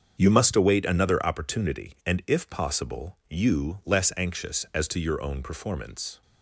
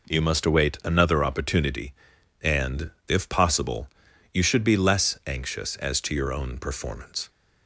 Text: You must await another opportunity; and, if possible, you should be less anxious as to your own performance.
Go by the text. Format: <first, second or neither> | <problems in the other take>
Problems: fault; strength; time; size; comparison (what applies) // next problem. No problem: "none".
second | starts louder than the rest; until 1.2 s; 7 dB // skips "should be"; at 3.8 s